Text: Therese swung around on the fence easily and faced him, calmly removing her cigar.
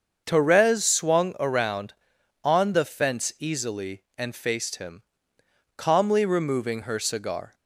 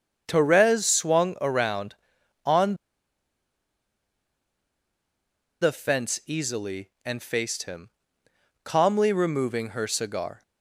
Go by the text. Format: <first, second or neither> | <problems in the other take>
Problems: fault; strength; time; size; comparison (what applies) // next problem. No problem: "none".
first | starts louder than the rest; until 1.2 s; 7 dB; also in the first // pauses between "on" and "the"; strong; at 2.7 s; 2.8 s long